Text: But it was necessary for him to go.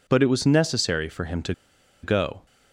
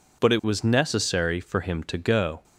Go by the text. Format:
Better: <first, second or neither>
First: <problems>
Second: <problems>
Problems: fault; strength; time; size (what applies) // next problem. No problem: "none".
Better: second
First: pauses between "to" and "go"; noticeable; at 1.5 s; 0.50 s long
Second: none